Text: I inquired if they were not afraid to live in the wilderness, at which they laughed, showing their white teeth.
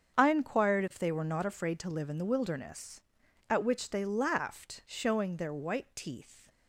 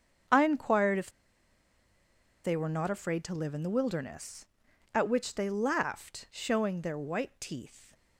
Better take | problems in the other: first | starts louder than the rest; strong; until 2.6 s; 7.5 dB; strong in the first // pauses between "if" and "they"; strong; at 1.0 s; 1.3 s long

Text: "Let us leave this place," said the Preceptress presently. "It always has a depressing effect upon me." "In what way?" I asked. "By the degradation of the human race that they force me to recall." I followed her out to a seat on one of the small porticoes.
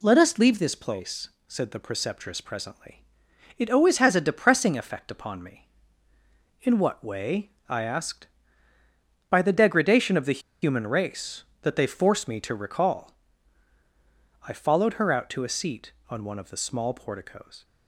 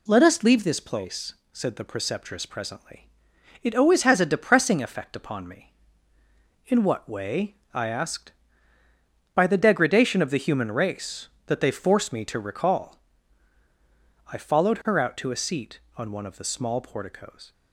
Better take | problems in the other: second | pauses between "the" and "human"; slight; at 10.4 s; 0.21 s long

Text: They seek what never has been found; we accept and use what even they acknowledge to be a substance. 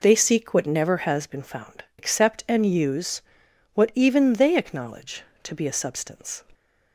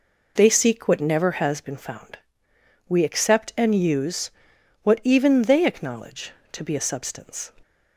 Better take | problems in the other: second | skips "we"; at 1.9 s // pauses between "use" and "what"; noticeable; at 3.2 s; 0.52 s long; noticeable in the second

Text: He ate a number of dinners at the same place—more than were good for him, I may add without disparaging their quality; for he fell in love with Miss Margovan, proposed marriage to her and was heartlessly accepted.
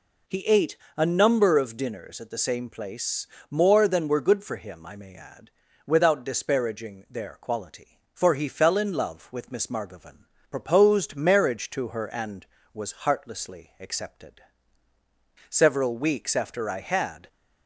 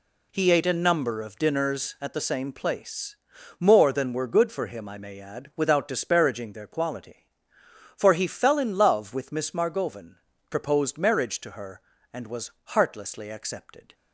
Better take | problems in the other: second | pauses between "ate" and "a"; slight; at 0.7 s; 0.20 s long // pauses between "add" and "without"; at 5.5 s; 0.38 s long // goes on to say "Several weeks after I had"; strong; from 15.4 s on; 1.8 s long

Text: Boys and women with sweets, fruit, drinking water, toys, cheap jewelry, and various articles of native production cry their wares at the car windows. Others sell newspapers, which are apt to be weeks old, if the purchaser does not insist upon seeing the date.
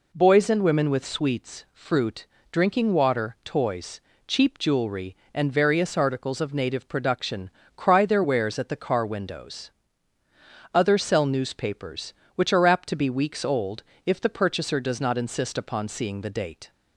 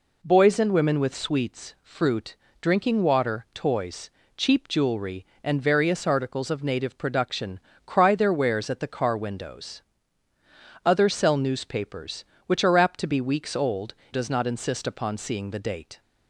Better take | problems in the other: first | pauses between "production" and "cry"; slight; at 7.5 s; 0.30 s long; slight in the first // skips "if the purchaser"; at 14.0 s

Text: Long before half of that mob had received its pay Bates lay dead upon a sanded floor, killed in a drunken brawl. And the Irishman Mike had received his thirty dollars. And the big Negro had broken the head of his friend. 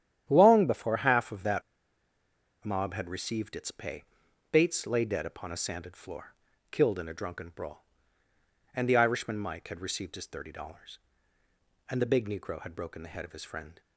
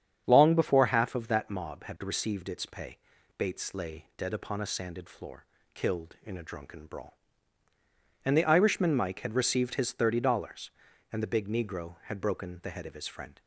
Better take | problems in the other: second | starts louder than the rest; strong; until 1.2 s; 10.5 dB; strong in the second // pauses between "that" and "mob"; at 1.6 s; 1.0 s long // pauses between "pay" and "Bates"; noticeable; at 4.0 s; 0.48 s long; also in the second

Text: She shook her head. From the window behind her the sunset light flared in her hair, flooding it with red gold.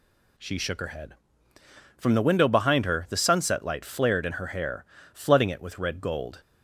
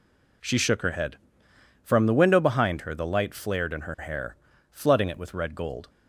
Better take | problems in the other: first | skips "sunset"; at 3.0 s

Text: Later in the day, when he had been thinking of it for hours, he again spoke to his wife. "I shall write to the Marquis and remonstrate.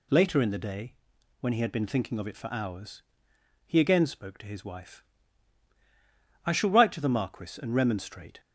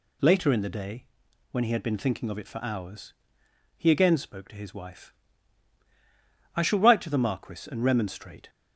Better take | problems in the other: neither | none

